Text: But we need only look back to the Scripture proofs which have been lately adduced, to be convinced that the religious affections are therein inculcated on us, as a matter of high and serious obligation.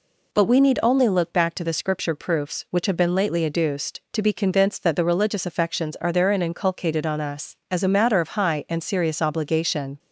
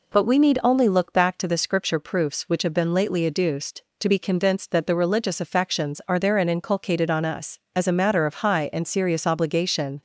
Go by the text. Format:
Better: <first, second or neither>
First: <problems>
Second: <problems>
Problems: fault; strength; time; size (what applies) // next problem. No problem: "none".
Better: neither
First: none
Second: none